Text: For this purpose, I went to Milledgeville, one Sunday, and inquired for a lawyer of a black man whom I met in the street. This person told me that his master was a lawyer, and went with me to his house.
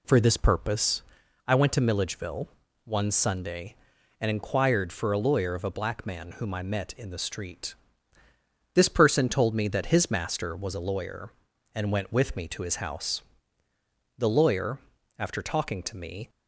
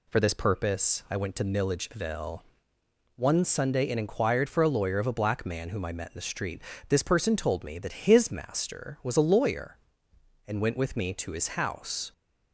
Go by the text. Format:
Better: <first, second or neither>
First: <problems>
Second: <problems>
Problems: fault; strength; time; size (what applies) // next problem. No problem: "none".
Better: second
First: goes on to say "The lawyer after talking to me"; strong; from 14.1 s on; 2.1 s long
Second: none